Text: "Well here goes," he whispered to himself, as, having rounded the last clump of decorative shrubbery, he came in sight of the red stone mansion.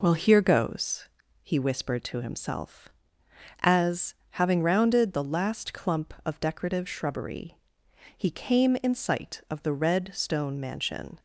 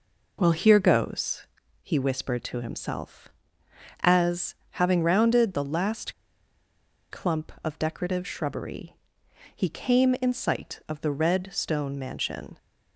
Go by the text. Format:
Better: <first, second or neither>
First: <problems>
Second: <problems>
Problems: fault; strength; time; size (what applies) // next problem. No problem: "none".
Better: first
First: none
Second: pauses between "last" and "clump"; noticeable; at 6.1 s; 0.98 s long